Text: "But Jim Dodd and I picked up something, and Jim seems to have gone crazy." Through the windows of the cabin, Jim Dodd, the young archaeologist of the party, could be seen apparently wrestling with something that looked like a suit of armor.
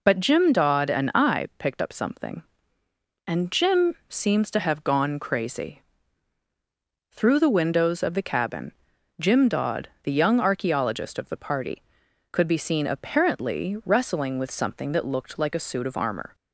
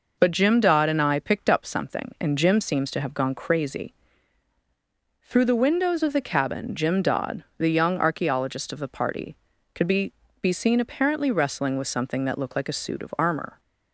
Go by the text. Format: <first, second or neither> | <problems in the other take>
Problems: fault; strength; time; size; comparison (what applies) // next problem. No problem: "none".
first | says "be" twice; at 10.4 s